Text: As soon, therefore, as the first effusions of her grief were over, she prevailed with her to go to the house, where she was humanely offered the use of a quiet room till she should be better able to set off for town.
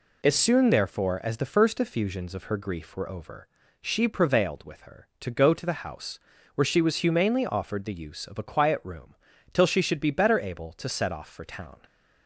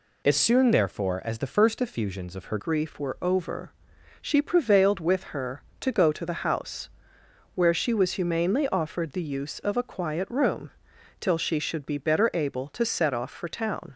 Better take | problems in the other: first | changes voice at "grief"; from 2.5 s on; 11.4 s long // pauses between "room" and "till"; noticeable; at 10.7 s; 0.48 s long; also in the first

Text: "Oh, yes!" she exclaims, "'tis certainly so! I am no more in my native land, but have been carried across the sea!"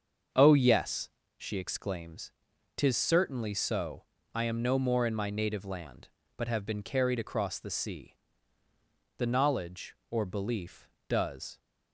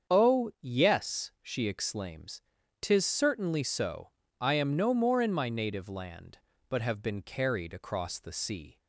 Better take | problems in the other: second | starts louder than the rest; until 1.6 s; 7 dB; strong in the second // goes on to say "The knowledge or belief does"; strong; from 9.1 s on; 2.4 s long

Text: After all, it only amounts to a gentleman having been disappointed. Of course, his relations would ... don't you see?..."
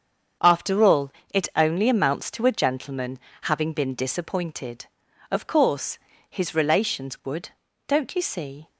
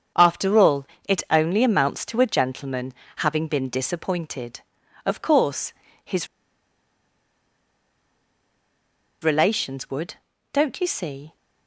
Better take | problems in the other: first | starts louder than the rest; strong; until 1.4 s; 7 dB; strong in the first // pauses between "gentleman" and "having"; slight; at 2.9 s; 0.24 s long; slight in the first // pauses between "his" and "relations"; strong; at 6.2 s; 2.9 s long

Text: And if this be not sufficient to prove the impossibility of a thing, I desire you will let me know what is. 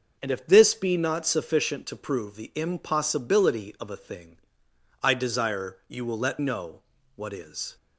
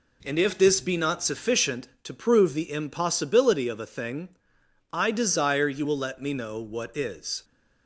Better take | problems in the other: second | starts louder than the rest; noticeable; until 1.2 s; 6 dB // skips "me"; at 6.3 s // pauses between "know" and "what"; slight; at 6.8 s; 0.34 s long

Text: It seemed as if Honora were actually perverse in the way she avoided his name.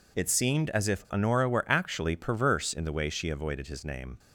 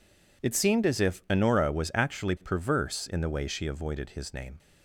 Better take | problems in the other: first | says "was" for "were"; at 1.6 s

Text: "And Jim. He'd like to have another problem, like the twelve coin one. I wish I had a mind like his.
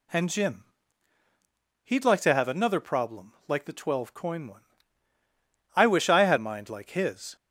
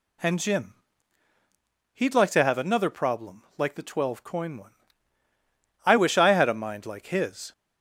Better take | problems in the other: second | skips "a"; at 6.3 s

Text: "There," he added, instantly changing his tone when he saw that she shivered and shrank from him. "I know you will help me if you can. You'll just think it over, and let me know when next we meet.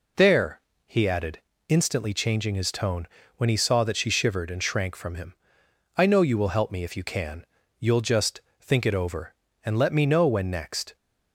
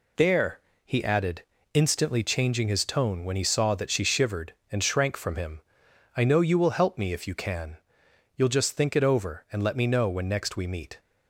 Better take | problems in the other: second | pauses between "tone" and "when"; slight; at 3.0 s; 0.30 s long // pauses between "just" and "think"; slight; at 8.4 s; 0.18 s long // stops before "we meet"; at 10.9 s

